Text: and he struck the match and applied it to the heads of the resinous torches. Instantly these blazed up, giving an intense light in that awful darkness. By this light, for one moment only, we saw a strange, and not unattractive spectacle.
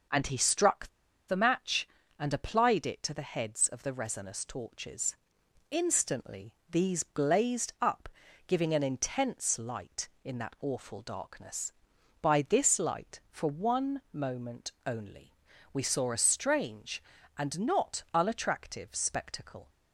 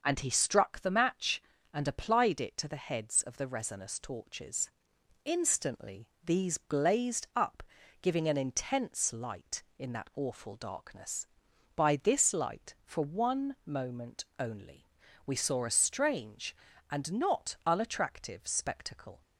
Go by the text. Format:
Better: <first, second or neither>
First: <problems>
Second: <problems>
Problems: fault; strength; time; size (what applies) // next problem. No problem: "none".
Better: second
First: starts louder than the rest; noticeable; until 1.5 s; 6 dB // pauses between "struck" and "the"; at 0.8 s; 0.39 s long // pauses between "Instantly" and "these"; slight; at 6.5 s; 0.18 s long // pauses between "moment" and "only"; slight; at 14.7 s; 0.16 s long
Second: pauses between "Instantly" and "these"; slight; at 6.0 s; 0.18 s long // pauses between "moment" and "only"; slight; at 14.2 s; 0.16 s long